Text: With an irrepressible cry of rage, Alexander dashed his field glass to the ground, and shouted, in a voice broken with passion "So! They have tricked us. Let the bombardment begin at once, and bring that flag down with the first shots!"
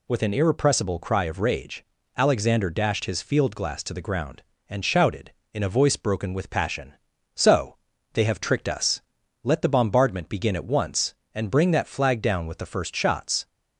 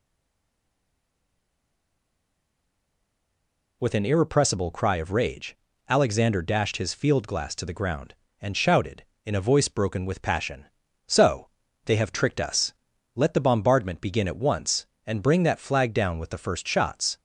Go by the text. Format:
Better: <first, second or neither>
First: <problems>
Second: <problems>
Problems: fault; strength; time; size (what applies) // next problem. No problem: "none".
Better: first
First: none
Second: stays silent before the first word; strong; until 3.8 s; 3.8 s long